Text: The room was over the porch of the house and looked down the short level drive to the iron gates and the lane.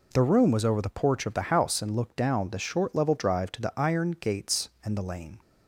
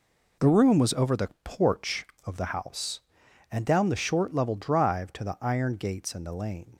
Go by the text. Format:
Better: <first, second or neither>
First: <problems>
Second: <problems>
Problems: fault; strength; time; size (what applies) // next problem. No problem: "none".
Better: first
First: none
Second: skips "looked"; at 3.6 s